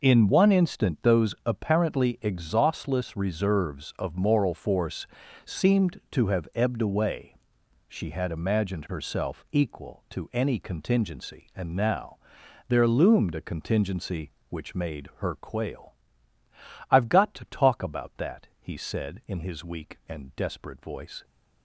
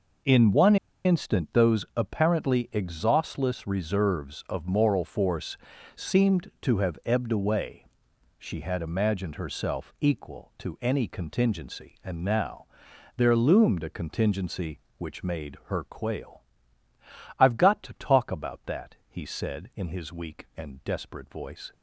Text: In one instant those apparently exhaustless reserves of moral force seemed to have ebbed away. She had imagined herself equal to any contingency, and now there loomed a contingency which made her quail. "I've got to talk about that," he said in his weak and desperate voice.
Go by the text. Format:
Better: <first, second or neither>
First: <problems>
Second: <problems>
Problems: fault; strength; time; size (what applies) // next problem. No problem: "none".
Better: first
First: pauses between "force" and "seemed"; at 5.0 s; 0.40 s long // pauses between "now" and "there"; noticeable; at 12.1 s; 0.50 s long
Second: pauses between "one" and "instant"; slight; at 0.7 s; 0.29 s long // pauses between "force" and "seemed"; at 5.5 s; 0.40 s long // pauses between "now" and "there"; noticeable; at 12.6 s; 0.50 s long